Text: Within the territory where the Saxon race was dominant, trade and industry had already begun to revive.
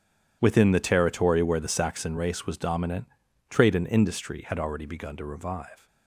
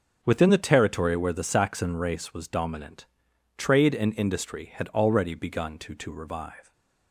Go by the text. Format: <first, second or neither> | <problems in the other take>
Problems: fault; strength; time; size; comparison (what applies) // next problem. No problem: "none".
first | starts louder than the rest; until 1.2 s; 6 dB // says "to" twice; at 5.9 s